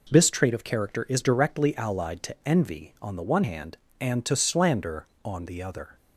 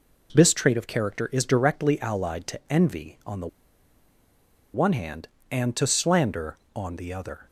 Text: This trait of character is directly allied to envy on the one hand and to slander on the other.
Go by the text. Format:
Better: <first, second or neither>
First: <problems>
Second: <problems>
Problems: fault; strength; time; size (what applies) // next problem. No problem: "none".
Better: first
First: none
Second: pauses between "the" and "one"; strong; at 3.4 s; 1.2 s long